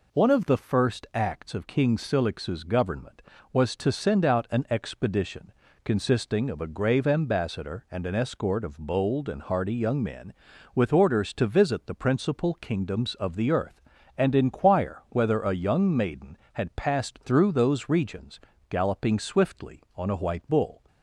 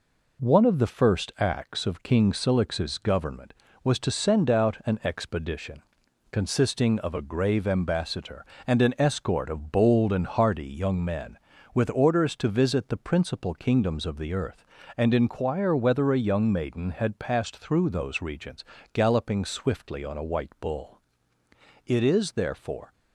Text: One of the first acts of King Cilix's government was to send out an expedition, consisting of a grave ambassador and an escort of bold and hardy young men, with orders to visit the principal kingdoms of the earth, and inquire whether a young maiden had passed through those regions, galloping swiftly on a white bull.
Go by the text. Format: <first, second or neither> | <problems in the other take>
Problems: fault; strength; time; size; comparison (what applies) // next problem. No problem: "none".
first | goes on to say "It is therefore"; noticeable; from 21.8 s on; 1.0 s long